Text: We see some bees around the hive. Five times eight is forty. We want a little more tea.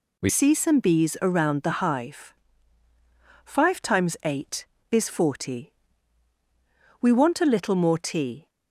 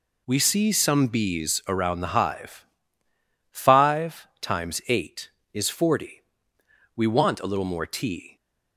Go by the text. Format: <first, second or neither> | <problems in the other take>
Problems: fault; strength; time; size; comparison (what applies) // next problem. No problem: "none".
second | changes voice at "see"; from 0.2 s on; 8.2 s long